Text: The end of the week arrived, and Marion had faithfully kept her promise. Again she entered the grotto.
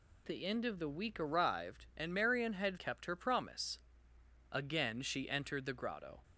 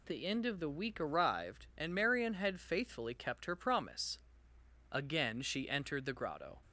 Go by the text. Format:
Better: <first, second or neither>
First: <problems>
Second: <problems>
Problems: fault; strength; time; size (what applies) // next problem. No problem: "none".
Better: second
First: skips "faithfully"; at 2.7 s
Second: none